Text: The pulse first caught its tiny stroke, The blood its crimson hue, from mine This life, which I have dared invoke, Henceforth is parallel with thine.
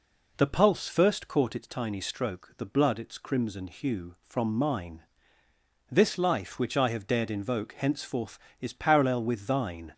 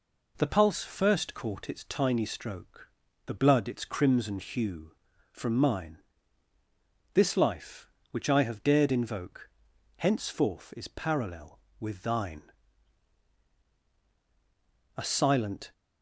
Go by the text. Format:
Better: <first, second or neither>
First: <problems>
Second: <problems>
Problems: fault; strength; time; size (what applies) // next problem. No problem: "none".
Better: first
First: pauses between "mine" and "This"; noticeable; at 5.0 s; 0.88 s long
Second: pauses between "mine" and "This"; at 5.9 s; 1.1 s long // goes on to say "A silent"; noticeable; from 14.9 s on; 0.74 s long